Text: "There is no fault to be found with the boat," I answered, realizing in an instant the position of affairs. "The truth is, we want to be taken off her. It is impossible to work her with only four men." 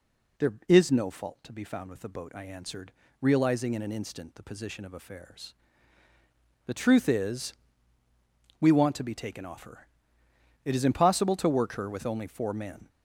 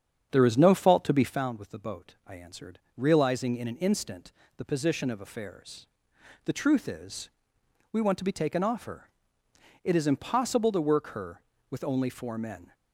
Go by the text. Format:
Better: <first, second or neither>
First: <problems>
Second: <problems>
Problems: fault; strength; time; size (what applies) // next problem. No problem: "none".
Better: first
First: none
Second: starts louder than the rest; strong; until 1.5 s; 8 dB // pauses between "instant" and "the"; slight; at 4.2 s; 0.28 s long